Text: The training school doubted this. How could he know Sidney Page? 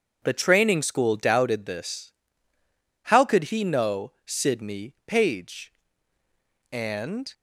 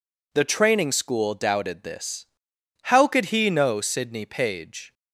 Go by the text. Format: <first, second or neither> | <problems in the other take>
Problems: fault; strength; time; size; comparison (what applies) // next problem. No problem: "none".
second | goes on to say "And"; noticeable; from 6.7 s on; 0.62 s long